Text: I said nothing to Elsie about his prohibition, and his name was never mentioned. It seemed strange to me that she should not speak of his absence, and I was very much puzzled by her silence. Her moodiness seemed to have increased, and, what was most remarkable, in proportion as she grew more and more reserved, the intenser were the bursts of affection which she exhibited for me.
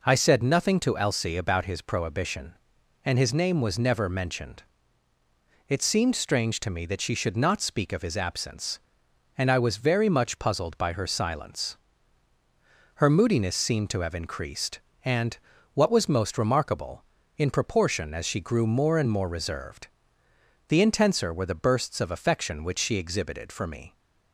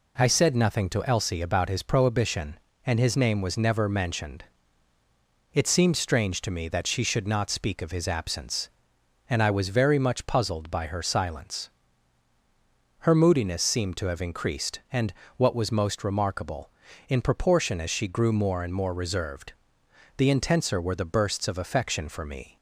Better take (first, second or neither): first